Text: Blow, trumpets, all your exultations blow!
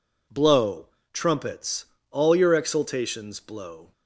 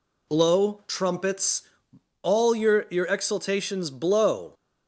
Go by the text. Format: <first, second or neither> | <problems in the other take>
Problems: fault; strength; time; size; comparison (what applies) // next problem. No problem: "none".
first | says "your" twice; at 2.9 s